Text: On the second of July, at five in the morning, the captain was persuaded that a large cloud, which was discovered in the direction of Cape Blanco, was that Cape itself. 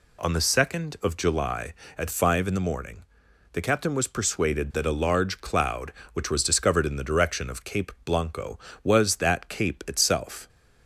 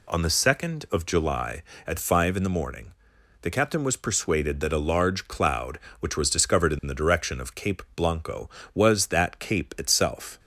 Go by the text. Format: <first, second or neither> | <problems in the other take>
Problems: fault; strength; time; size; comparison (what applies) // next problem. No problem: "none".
neither | none